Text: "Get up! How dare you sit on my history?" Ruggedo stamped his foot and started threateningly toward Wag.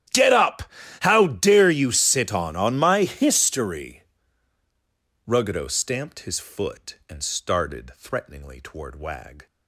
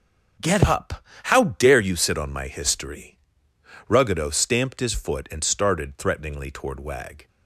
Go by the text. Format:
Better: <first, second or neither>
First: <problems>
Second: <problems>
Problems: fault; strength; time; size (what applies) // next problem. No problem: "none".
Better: second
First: starts louder than the rest; strong; until 1.4 s; 11.5 dB // says "on" twice; at 2.5 s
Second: none